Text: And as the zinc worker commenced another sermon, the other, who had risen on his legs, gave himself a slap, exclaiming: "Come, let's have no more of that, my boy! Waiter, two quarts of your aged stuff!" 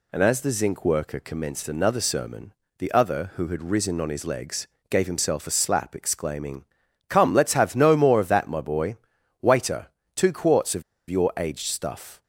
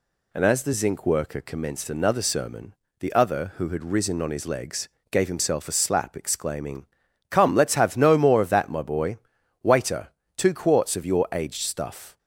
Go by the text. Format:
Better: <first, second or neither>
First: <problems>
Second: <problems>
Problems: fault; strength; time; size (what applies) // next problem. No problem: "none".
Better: second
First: pauses between "of" and "your"; slight; at 10.8 s; 0.27 s long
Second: none